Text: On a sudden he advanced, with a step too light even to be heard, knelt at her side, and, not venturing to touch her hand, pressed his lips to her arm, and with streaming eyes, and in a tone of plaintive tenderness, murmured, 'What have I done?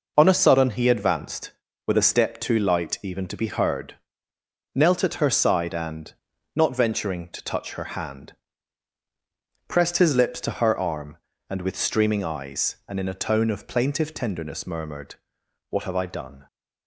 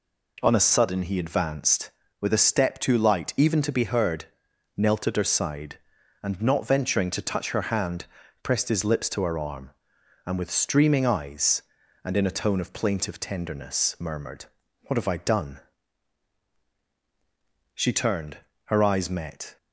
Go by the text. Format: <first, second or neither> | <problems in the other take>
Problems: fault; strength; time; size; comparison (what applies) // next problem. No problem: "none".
first | goes on to say "She turned her eyes met"; strong; from 17.7 s on; 1.8 s long